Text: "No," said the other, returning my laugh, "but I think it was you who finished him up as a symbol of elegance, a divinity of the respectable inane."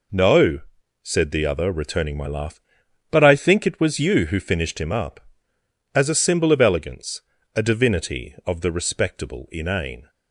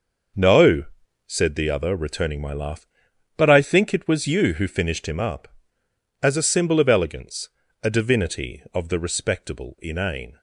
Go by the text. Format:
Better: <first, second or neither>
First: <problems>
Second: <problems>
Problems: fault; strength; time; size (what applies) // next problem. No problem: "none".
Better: first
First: none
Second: starts louder than the rest; noticeable; until 1.5 s; 6 dB